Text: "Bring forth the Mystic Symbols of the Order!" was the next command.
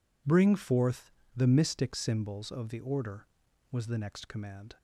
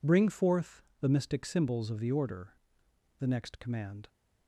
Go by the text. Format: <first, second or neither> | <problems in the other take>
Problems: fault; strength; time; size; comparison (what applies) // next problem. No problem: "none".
first | pauses between "forth" and "the"; slight; at 0.8 s; 0.18 s long; slight in the first // skips "was"; at 2.8 s